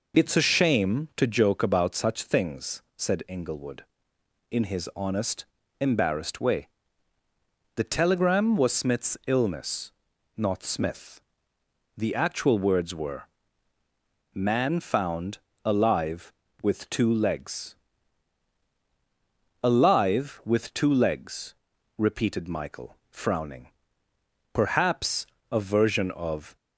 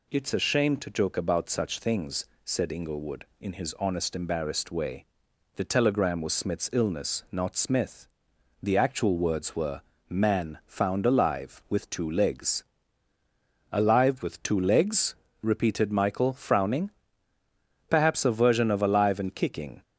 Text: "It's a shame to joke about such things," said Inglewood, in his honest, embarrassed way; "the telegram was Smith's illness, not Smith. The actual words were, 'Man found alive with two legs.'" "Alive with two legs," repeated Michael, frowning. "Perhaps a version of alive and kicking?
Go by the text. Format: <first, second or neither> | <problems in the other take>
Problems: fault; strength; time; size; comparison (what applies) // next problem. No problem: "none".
second | pauses between "found" and "alive"; slight; at 15.3 s; 0.26 s long // pauses between "Perhaps" and "a"; slight; at 25.2 s; 0.26 s long // stops before "alive and kicking"; at 26.5 s